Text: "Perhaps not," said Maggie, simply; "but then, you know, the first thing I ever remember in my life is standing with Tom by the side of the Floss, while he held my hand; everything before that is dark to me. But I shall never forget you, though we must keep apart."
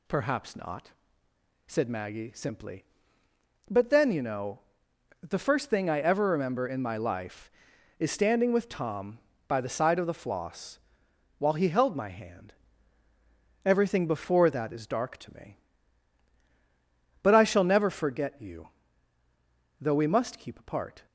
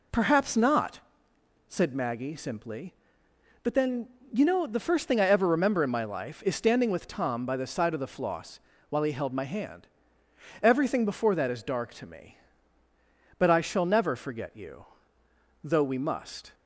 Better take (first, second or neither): first